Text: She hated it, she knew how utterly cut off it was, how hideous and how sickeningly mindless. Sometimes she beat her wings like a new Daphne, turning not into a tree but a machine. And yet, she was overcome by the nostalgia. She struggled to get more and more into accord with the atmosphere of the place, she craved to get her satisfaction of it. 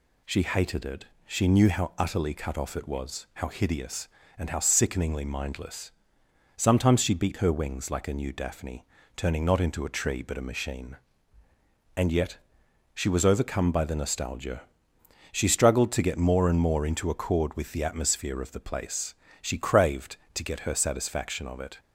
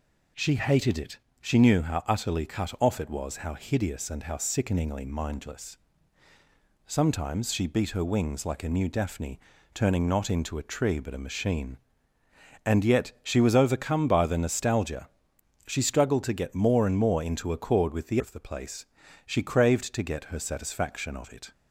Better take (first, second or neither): first